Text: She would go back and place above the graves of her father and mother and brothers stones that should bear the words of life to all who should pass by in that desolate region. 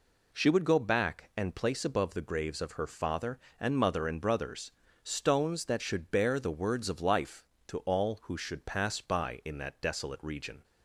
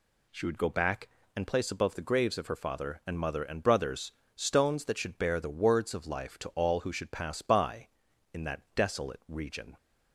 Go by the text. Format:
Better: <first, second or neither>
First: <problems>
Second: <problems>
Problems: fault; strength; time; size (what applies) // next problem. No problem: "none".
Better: neither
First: pauses between "brothers" and "stones"; slight; at 4.7 s; 0.32 s long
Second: pauses between "brothers" and "stones"; slight; at 4.1 s; 0.26 s long